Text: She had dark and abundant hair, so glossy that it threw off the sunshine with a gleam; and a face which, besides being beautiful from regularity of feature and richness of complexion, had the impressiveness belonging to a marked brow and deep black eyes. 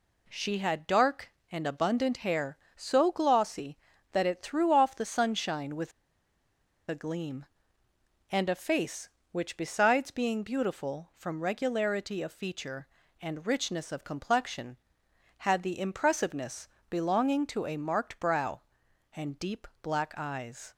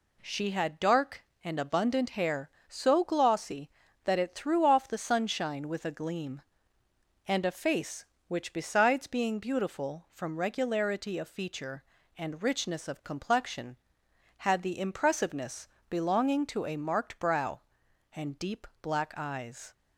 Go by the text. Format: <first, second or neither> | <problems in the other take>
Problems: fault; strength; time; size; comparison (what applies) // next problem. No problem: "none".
second | pauses between "with" and "a"; noticeable; at 5.9 s; 0.97 s long // pauses between "impressiveness" and "belonging"; slight; at 16.6 s; 0.22 s long; slight in the second // pauses between "deep" and "black"; slight; at 19.6 s; 0.16 s long; slight in the second